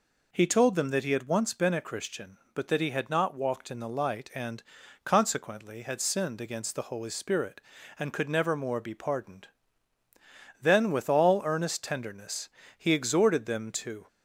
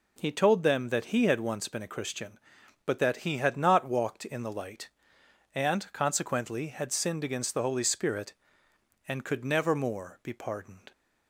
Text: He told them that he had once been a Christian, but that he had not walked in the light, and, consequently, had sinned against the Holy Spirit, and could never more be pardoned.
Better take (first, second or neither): second